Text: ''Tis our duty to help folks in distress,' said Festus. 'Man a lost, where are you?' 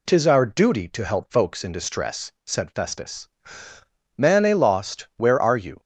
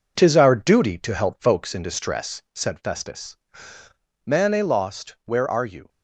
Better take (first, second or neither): first